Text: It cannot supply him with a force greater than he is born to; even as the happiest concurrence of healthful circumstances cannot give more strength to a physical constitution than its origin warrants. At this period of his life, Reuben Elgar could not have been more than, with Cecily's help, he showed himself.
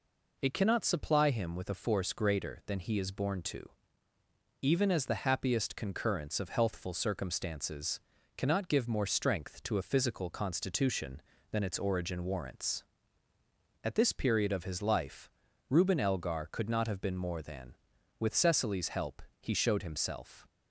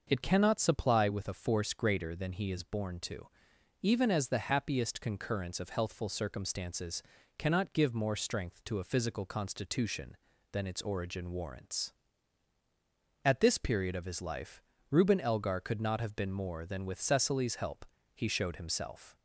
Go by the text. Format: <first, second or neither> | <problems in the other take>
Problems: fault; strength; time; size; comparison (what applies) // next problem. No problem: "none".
first | starts louder than the rest; noticeable; until 1.0 s; 6 dB // skips "him"; at 1.0 s // pauses between "circumstances" and "cannot"; slight; at 7.0 s; 0.34 s long; also in the first